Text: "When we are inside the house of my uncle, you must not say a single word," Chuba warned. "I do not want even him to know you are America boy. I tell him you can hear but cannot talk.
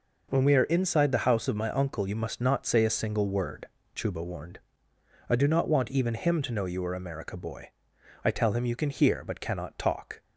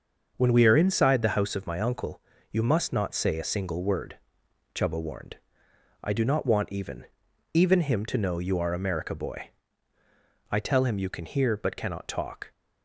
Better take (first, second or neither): first